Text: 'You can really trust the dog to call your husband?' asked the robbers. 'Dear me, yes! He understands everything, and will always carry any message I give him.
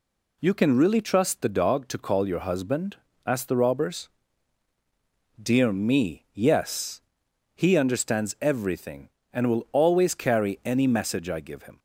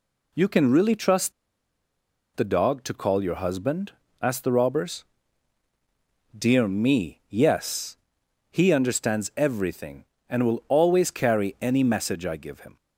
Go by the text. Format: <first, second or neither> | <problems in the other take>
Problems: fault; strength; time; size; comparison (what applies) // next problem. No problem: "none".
first | pauses between "trust" and "the"; at 1.3 s; 1.0 s long